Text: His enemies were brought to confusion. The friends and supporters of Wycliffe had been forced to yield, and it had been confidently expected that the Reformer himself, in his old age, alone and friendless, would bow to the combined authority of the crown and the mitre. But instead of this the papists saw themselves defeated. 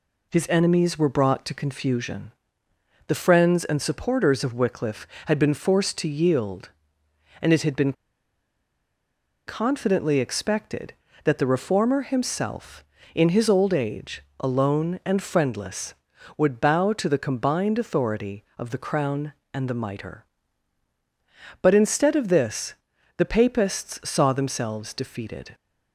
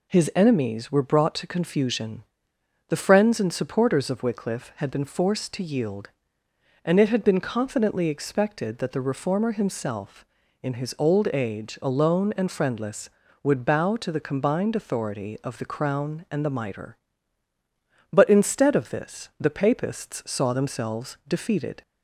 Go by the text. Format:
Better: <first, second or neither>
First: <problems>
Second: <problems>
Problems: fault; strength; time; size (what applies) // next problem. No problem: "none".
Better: second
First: pauses between "been" and "confidently"; strong; at 7.9 s; 1.5 s long // pauses between "this" and "the"; at 22.7 s; 0.42 s long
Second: none